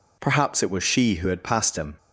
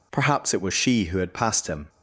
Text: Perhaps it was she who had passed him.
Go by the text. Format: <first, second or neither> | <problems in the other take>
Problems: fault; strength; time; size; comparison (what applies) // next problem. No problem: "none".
neither | none